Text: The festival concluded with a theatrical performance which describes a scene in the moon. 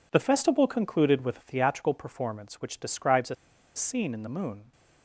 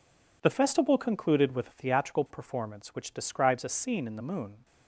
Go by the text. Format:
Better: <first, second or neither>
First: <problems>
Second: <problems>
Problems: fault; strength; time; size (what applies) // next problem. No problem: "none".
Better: second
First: pauses between "a" and "scene"; at 3.3 s; 0.40 s long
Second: none